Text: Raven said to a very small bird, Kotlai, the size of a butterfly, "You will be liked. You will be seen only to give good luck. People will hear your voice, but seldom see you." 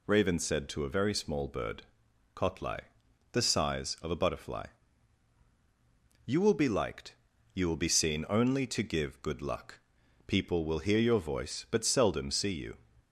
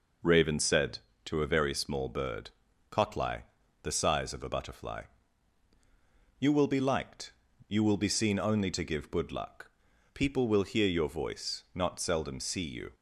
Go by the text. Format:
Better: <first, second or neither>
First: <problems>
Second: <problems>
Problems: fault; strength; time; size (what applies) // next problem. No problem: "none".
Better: first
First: none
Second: says "not" for "but"; at 11.7 s